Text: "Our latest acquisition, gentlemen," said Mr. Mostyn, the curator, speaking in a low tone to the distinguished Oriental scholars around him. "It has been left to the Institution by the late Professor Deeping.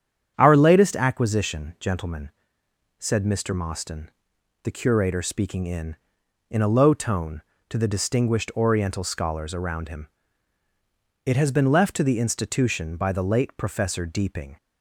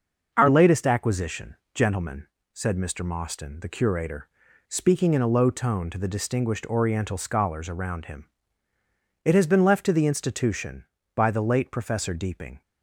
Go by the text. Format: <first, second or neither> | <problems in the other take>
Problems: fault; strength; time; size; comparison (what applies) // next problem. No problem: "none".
second | starts louder than the rest; strong; until 1.3 s; 8.5 dB; noticeable in the second // says "in" twice; at 6.4 s